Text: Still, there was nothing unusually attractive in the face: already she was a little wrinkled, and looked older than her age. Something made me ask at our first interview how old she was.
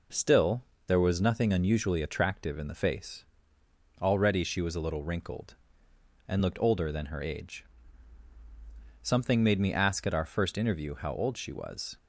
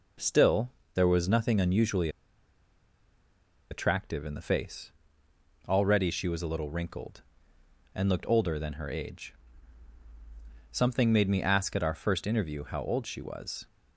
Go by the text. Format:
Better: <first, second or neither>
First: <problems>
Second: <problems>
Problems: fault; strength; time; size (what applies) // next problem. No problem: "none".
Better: first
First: none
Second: pauses between "unusually" and "attractive"; strong; at 2.0 s; 1.6 s long